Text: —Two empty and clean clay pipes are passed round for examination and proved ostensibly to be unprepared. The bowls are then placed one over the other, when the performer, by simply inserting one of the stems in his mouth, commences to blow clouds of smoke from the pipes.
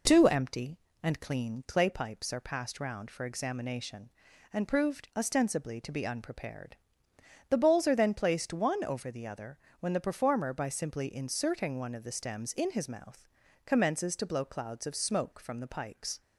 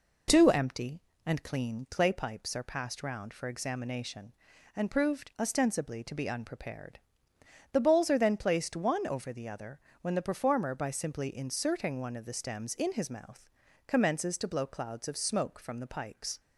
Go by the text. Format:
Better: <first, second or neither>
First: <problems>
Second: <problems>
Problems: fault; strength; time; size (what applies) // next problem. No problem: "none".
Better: neither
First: none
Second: none